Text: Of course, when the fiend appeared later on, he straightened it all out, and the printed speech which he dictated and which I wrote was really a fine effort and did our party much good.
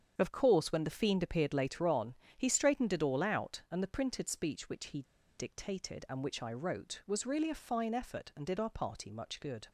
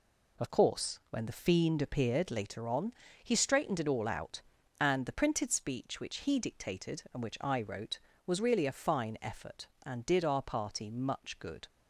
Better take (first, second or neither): second